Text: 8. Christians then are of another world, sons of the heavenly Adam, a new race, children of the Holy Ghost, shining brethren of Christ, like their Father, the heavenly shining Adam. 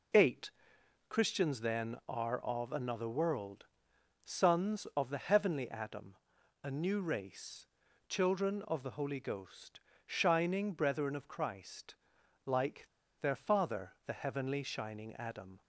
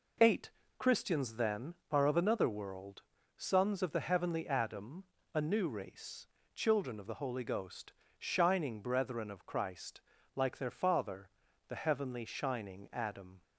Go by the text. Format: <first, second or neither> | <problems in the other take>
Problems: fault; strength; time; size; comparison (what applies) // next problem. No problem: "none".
second | pauses between "like" and "their"; slight; at 12.8 s; 0.33 s long